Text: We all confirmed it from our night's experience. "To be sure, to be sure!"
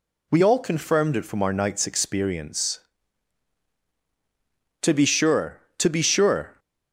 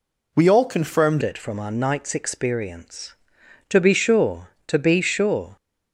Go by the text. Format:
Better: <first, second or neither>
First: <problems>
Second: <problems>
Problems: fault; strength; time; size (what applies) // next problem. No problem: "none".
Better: first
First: none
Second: changes voice at "it"; from 1.2 s on; 4.3 s long